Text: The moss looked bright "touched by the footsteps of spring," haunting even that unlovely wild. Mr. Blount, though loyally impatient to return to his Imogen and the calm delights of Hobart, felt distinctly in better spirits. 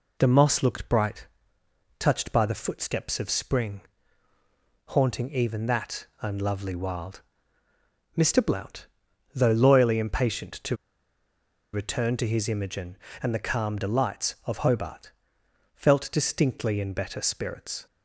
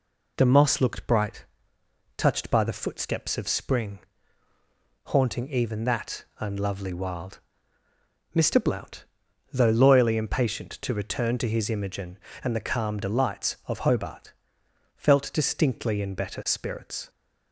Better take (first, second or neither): second